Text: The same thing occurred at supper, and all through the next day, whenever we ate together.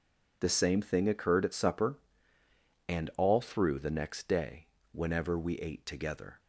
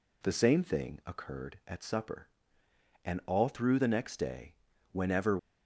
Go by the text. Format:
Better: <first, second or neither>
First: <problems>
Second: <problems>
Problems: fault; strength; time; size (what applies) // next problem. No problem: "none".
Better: first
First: none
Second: stops before "we ate together"; at 5.3 s